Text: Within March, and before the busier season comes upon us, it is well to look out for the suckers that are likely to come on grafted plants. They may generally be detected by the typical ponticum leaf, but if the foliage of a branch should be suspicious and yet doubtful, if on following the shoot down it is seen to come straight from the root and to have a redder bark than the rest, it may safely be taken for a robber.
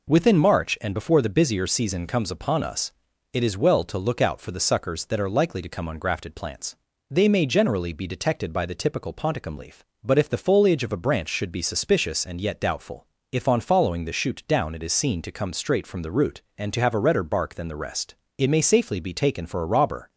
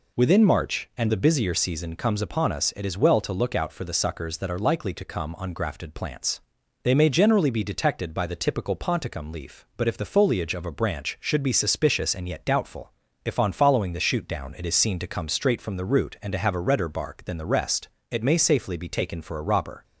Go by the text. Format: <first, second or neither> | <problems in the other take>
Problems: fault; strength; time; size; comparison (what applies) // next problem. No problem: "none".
first | skips "before"; at 1.0 s